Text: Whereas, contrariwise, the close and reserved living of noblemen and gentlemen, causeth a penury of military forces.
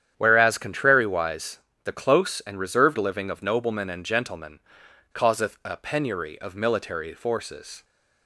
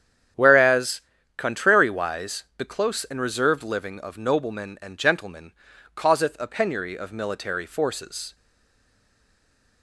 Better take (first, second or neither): first